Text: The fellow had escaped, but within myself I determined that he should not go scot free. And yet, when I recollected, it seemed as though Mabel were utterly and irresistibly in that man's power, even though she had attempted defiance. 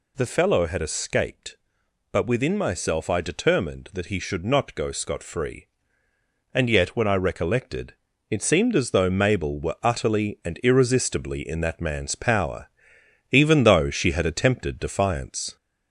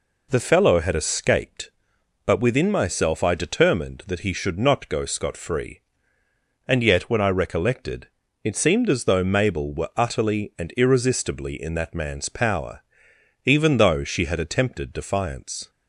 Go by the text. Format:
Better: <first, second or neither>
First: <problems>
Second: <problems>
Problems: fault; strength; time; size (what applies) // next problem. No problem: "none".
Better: second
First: gets louder; slight; throughout; 2.5 dB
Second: none